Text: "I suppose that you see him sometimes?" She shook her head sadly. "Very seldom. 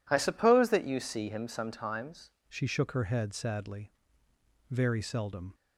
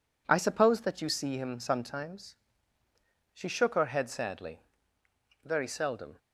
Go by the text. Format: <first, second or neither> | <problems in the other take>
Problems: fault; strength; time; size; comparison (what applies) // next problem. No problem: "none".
second | changes voice at "She"; from 2.4 s on; 3.1 s long